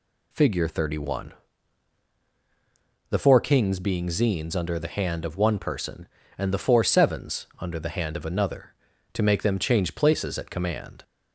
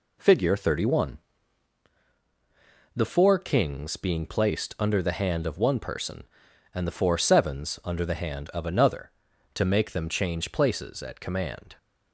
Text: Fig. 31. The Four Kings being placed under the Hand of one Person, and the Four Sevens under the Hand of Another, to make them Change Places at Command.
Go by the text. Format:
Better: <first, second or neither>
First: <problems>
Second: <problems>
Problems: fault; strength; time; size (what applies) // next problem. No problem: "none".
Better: second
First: says "zines" for "placed"; at 4.0 s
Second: none